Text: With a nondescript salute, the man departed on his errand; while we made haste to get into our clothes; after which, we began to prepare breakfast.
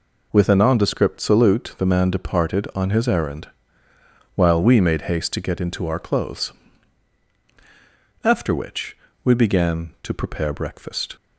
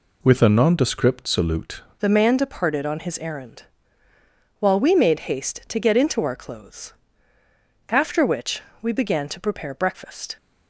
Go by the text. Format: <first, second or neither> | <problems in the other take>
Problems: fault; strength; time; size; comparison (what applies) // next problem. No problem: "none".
first | changes voice at "the"; from 1.9 s on; 8.4 s long